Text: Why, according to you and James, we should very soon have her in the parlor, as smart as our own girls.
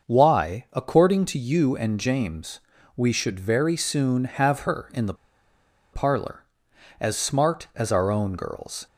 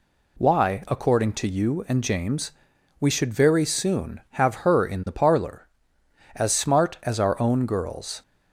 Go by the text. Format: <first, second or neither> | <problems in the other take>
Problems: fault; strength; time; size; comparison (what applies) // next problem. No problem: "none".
second | starts louder than the rest; until 1.1 s; 6.5 dB // pauses between "the" and "parlor"; noticeable; at 5.1 s; 0.79 s long